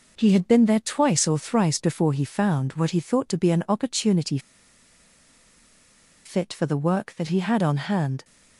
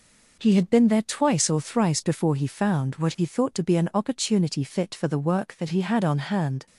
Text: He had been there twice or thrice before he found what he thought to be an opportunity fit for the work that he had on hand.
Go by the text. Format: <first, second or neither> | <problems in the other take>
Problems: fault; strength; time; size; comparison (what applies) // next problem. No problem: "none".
second | pauses between "opportunity" and "fit"; strong; at 4.3 s; 1.8 s long